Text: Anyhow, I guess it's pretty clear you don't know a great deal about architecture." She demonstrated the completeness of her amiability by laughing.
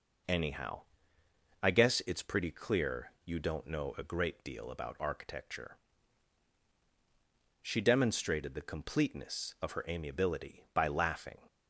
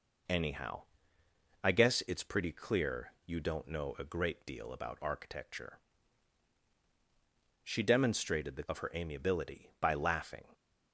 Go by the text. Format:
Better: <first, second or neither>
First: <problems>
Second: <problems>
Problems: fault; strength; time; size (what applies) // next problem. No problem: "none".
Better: first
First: pauses between "clear" and "you"; slight; at 3.1 s; 0.16 s long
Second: pauses between "clear" and "you"; slight; at 3.1 s; 0.16 s long // skips "completeness"; at 8.6 s